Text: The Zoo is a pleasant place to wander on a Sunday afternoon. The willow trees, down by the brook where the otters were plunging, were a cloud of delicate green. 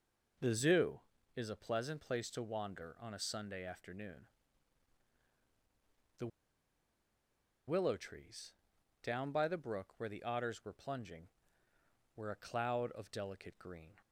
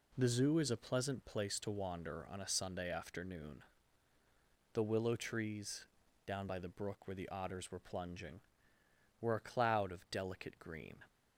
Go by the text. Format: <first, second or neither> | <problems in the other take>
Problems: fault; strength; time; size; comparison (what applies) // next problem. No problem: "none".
second | pauses between "The" and "willow"; strong; at 6.2 s; 1.4 s long